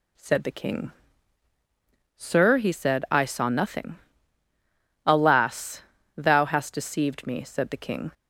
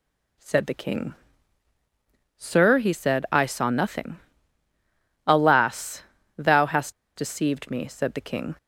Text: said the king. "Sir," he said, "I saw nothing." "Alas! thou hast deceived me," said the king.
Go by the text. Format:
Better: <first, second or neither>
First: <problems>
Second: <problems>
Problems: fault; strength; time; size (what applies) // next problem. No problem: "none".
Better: first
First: none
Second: pauses between "hast" and "deceived"; slight; at 6.9 s; 0.25 s long